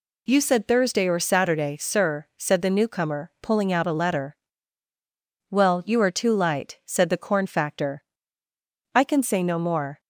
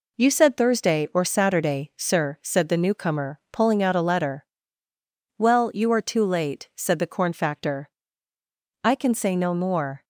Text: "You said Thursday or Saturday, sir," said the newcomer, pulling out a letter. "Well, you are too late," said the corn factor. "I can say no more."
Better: second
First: says "light" for "late"; at 6.3 s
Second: none

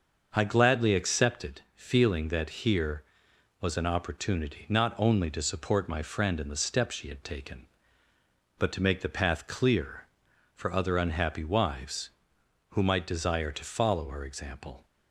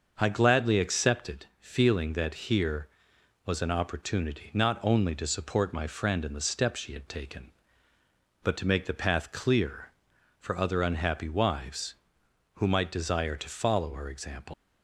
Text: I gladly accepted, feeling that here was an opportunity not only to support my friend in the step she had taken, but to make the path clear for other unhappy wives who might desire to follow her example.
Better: first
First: starts louder than the rest; until 1.3 s; 6.5 dB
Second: starts louder than the rest; until 1.1 s; 6.5 dB // leaves "example" unfinished; at 14.5 s; 155 ms

